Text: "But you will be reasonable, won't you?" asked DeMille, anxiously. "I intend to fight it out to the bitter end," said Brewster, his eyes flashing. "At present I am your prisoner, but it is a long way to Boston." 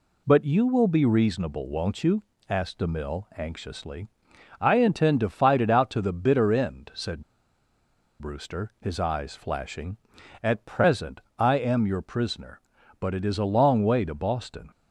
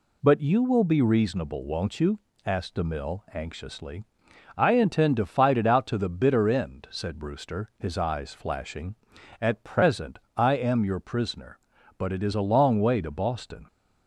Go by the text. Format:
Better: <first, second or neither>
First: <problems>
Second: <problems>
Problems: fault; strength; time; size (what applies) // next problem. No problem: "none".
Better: second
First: pauses between "said" and "Brewster"; at 7.2 s; 0.99 s long // pauses between "present" and "I"; slight; at 11.2 s; 0.18 s long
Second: pauses between "present" and "I"; slight; at 10.1 s; 0.18 s long